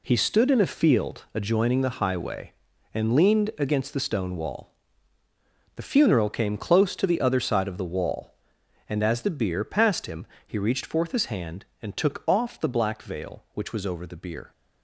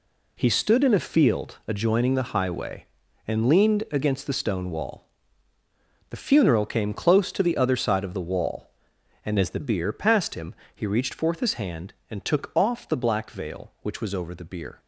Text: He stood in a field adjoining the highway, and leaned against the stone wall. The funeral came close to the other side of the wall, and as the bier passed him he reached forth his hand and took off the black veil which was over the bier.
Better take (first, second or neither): first